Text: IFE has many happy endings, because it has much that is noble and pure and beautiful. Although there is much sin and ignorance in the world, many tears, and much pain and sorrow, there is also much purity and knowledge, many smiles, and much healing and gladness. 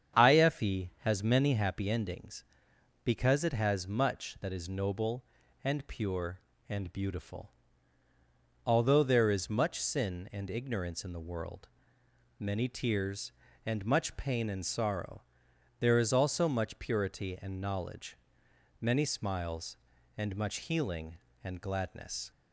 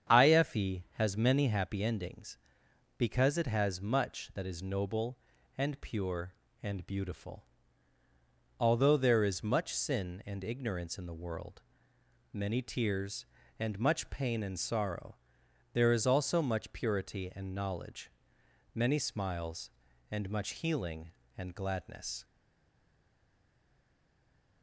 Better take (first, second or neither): first